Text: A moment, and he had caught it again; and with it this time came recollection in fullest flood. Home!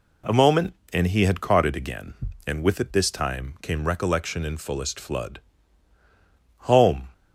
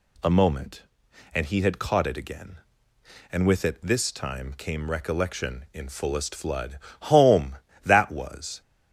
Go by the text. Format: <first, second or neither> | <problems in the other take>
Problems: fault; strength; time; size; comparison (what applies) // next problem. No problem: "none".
first | goes on to say "That was"; noticeable; from 7.8 s on; 0.76 s long